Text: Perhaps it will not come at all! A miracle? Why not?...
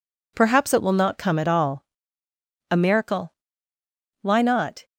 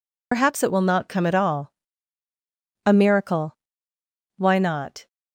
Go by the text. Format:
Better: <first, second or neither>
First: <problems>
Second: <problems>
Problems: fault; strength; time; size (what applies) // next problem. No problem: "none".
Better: first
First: none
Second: loses the start of "Perhaps"; at 0.3 s; 85 ms